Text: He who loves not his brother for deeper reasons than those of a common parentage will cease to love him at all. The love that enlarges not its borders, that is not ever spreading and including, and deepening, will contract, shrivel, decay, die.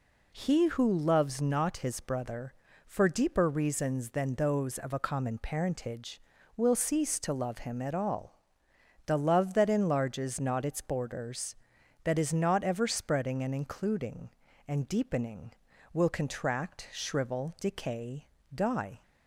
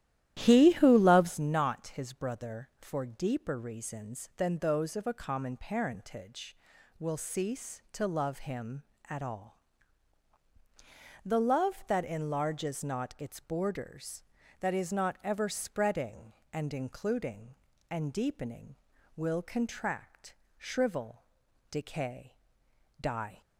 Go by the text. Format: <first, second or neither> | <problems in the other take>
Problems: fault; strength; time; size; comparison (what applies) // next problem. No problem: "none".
first | starts louder than the rest; strong; until 1.4 s; 13 dB